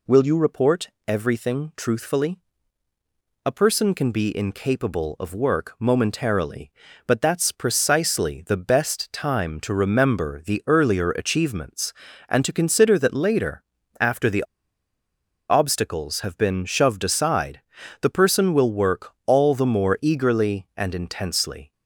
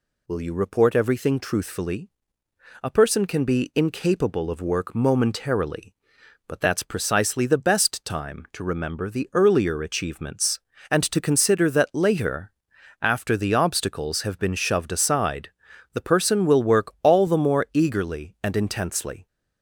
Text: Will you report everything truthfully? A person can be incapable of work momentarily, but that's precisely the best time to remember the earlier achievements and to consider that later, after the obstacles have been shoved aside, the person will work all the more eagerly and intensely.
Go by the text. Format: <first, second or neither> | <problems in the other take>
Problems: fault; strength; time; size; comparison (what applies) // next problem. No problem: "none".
second | pauses between "report" and "everything"; slight; at 0.8 s; 0.18 s long // pauses between "the" and "obstacles"; at 14.4 s; 1.0 s long